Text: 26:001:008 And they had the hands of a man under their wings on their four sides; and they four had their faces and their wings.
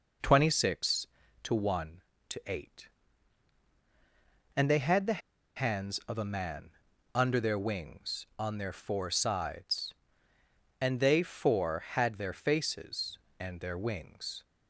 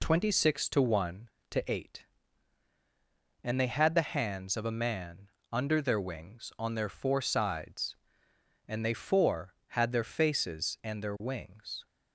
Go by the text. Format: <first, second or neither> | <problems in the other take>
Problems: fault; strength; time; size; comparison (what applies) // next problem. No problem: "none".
second | pauses between "the" and "hands"; at 5.1 s; 0.36 s long // pauses between "man" and "under"; at 6.7 s; 0.44 s long; slight in the second